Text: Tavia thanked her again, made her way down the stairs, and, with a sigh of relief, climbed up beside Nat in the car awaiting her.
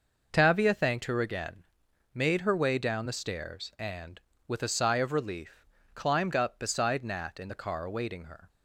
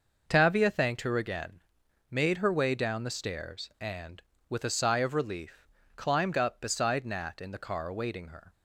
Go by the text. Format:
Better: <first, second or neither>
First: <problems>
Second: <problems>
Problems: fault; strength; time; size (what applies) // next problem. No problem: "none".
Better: neither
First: none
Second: none